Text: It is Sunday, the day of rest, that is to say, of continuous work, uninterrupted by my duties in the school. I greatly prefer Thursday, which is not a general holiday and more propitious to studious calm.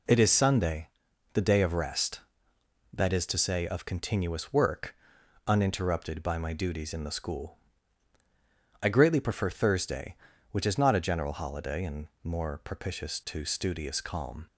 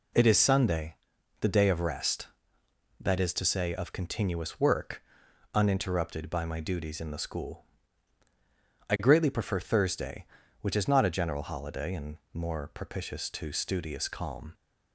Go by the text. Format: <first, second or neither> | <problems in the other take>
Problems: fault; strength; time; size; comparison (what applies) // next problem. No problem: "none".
neither | pauses between "and" and "more"; slight; the same in both